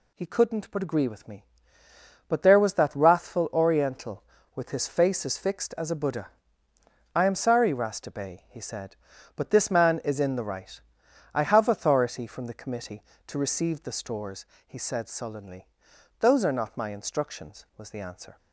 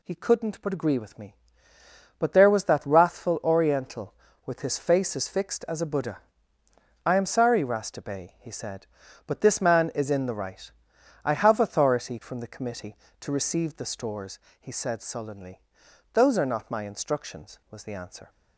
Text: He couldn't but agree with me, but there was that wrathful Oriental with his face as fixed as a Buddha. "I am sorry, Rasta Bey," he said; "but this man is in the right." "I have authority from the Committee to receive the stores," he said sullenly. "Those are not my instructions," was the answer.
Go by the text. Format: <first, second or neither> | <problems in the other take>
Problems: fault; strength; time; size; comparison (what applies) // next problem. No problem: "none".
neither | none